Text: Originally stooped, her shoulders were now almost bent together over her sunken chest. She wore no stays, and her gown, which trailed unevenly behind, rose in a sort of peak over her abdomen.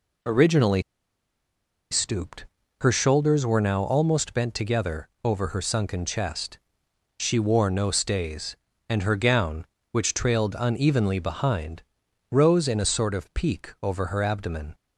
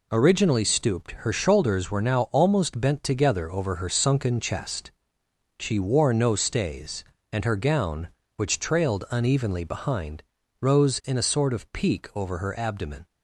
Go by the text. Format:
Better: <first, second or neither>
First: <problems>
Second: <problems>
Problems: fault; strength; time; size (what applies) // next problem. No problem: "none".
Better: second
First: pauses between "Originally" and "stooped"; at 0.8 s; 1.0 s long // pauses between "together" and "over"; slight; at 5.0 s; 0.16 s long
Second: none